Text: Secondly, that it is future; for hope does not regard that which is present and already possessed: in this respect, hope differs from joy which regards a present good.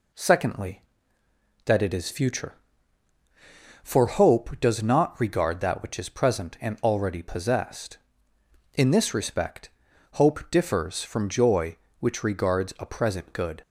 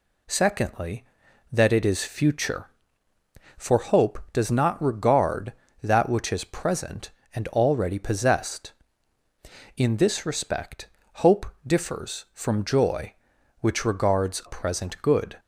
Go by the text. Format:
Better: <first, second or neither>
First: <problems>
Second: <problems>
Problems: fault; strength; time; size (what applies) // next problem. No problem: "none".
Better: first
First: none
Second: skips "a"; at 14.4 s